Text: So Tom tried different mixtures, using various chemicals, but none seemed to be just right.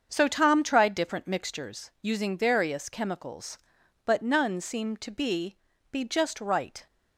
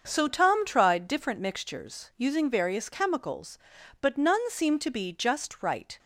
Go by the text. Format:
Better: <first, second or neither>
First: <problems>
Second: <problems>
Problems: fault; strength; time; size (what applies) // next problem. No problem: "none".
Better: second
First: starts louder than the rest; until 1.1 s; 7 dB // says "be" twice; at 5.9 s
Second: starts louder than the rest; until 1.0 s; 6.5 dB